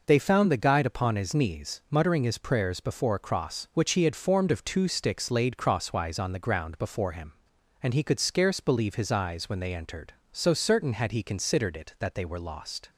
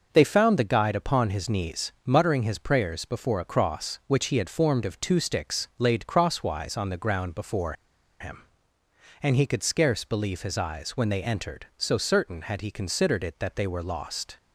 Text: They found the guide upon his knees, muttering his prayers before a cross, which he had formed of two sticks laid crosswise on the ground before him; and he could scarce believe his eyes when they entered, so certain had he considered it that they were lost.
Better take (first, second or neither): first